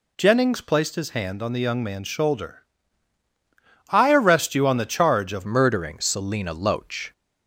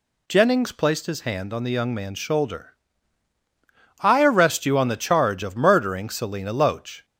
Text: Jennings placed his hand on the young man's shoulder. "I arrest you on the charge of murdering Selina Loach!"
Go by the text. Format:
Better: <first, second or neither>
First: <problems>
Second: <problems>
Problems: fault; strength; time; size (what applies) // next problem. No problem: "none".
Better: second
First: changes voice at "murdering"; from 5.4 s on; 1.7 s long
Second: none